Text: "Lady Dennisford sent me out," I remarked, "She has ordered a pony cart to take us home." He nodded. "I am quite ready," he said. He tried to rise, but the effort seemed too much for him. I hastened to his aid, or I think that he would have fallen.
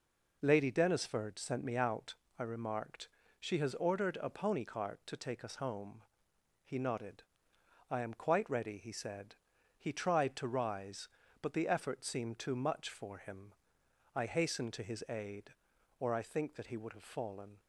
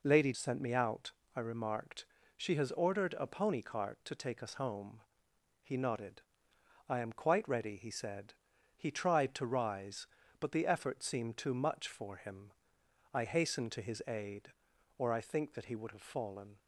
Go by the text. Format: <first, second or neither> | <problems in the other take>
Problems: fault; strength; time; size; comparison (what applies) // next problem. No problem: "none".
first | skips "Dennisford"; at 0.3 s